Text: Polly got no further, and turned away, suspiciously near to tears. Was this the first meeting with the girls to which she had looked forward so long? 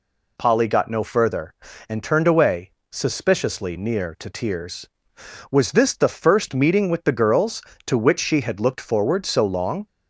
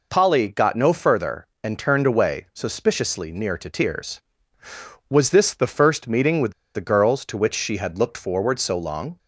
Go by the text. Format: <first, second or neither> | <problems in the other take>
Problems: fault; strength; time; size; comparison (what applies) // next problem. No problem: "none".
first | pauses between "with" and "the"; slight; at 6.5 s; 0.22 s long